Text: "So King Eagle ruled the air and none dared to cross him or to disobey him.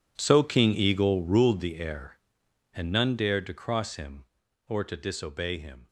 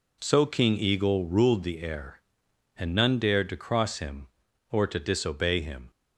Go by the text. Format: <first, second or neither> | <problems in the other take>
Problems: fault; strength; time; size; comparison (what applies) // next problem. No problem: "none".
second | gets quieter; strong; throughout; 16.5 dB